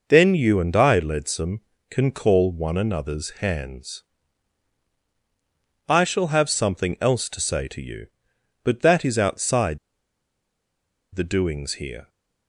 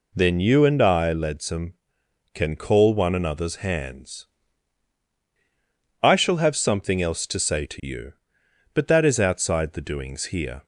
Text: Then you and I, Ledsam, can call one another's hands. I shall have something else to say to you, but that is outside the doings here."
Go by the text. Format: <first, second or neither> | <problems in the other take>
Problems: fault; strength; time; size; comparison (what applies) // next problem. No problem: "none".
second | pauses between "outside" and "the"; strong; at 9.7 s; 1.3 s long